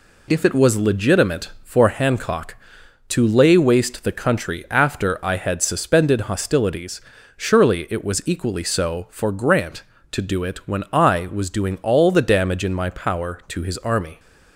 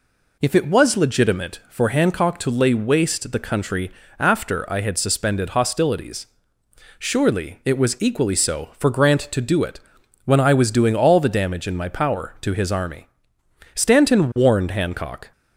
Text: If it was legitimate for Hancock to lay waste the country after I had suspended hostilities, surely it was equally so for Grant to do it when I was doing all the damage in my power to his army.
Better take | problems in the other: first | pauses between "country" and "after"; slight; at 3.8 s; 0.30 s long // pauses between "it" and "when"; noticeable; at 9.7 s; 0.46 s long // goes on to say "Stanton warned Hancock"; from 13.7 s on; 1.5 s long

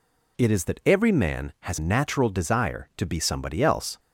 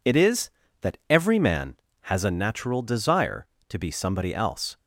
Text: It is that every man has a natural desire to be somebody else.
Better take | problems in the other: second | skips "a"; at 1.7 s

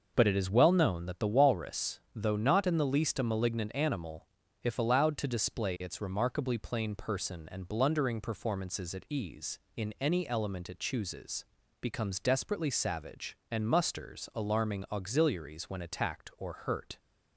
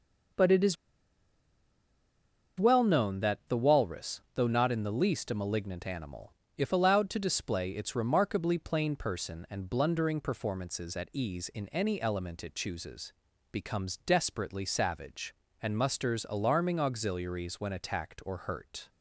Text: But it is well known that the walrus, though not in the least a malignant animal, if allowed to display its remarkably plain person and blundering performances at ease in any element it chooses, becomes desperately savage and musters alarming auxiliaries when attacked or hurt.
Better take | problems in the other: first | pauses between "is" and "well"; strong; at 0.7 s; 1.8 s long

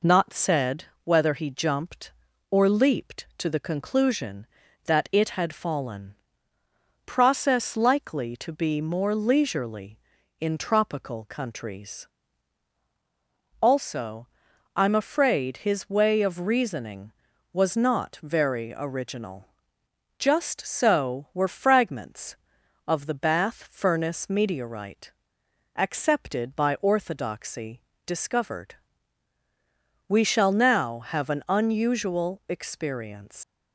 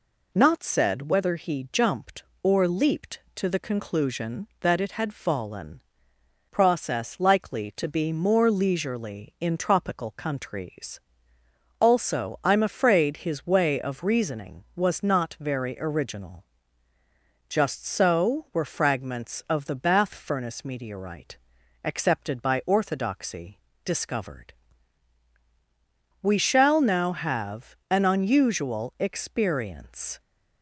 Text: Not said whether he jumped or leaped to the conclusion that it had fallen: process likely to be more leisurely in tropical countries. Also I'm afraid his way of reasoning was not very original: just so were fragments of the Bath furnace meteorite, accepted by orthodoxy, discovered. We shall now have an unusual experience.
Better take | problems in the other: second | pauses between "said" and "whether"; slight; at 0.8 s; 0.20 s long // pauses between "Also" and "I'm"; noticeable; at 14.2 s; 0.48 s long // leaves "experience" unfinished; at 33.4 s; 115 ms

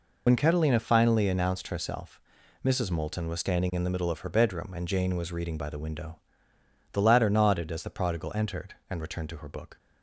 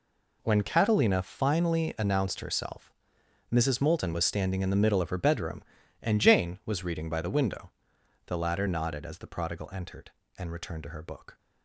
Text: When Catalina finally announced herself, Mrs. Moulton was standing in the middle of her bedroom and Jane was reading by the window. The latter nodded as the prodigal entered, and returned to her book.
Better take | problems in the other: second | loses the start of "When"; at 0.2 s; 65 ms

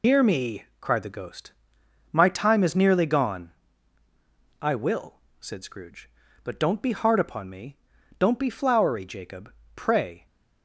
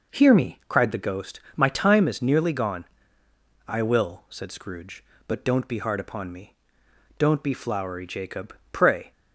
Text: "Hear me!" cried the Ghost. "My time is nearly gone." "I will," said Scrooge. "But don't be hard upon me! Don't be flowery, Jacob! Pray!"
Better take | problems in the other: second | loses the start of "Hear"; at 0.0 s; 130 ms

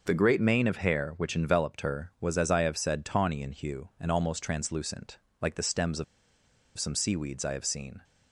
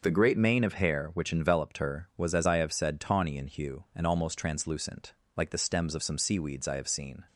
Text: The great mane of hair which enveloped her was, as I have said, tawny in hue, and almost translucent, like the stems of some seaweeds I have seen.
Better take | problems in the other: second | pauses between "of" and "some"; noticeable; at 6.0 s; 0.72 s long

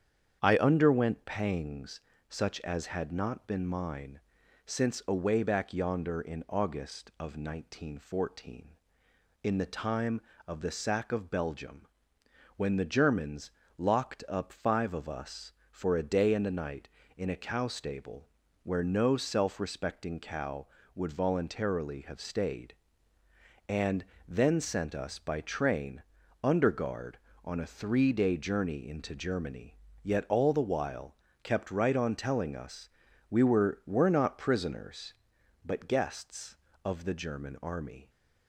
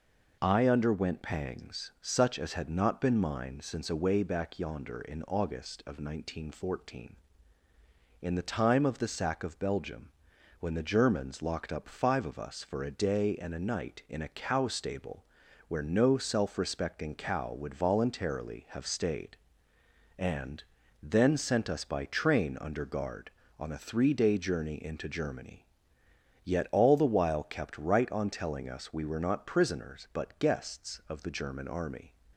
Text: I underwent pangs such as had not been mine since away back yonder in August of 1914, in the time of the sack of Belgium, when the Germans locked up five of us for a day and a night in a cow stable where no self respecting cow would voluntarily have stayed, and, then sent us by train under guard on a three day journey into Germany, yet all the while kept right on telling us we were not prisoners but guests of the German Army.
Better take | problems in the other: second | starts louder than the rest; strong; until 1.4 s; 8 dB // pauses between "pangs" and "such"; slight; at 1.9 s; 0.30 s long // pauses between "mine" and "since"; noticeable; at 4.1 s; 0.46 s long // pauses between "Germans" and "locked"; slight; at 13.5 s; 0.26 s long // pauses between "stable" and "where"; slight; at 18.2 s; 0.34 s long; also in the second // pauses between "train" and "under"; at 26.0 s; 0.40 s long // pauses between "while" and "kept"; slight; at 31.1 s; 0.28 s long // pauses between "us" and "we"; at 32.8 s; 0.40 s long // says "were" twice; at 33.8 s

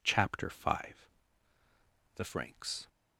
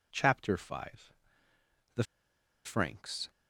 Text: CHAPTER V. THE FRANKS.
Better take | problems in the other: first | pauses between "THE" and "FRANKS"; noticeable; at 2.0 s; 0.62 s long

